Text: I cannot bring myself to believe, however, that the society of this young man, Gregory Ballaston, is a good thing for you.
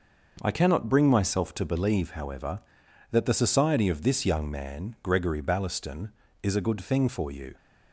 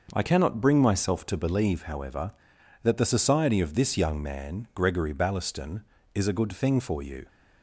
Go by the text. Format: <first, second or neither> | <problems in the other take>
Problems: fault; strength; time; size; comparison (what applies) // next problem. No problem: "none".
neither | starts louder than the rest; noticeable; the same in both